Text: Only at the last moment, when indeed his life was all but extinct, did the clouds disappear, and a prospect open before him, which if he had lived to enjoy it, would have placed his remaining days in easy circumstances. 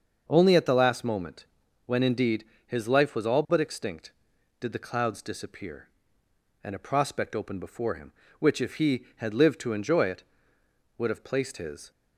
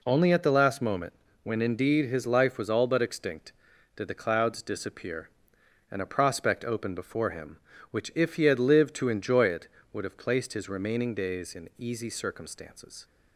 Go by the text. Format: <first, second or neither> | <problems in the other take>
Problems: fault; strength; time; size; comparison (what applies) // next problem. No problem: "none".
second | starts louder than the rest; until 1.2 s; 6.5 dB // pauses between "indeed" and "his"; slight; at 2.4 s; 0.22 s long // stops before "remaining days in easy circumstances"; at 11.9 s